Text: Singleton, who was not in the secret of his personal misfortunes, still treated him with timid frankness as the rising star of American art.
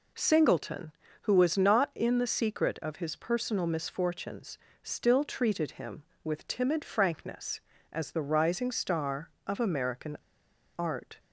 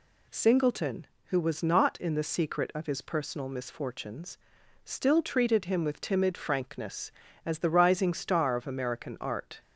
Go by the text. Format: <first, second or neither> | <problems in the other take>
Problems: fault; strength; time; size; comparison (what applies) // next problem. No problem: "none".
second | pauses between "American" and "art"; noticeable; at 10.1 s; 0.61 s long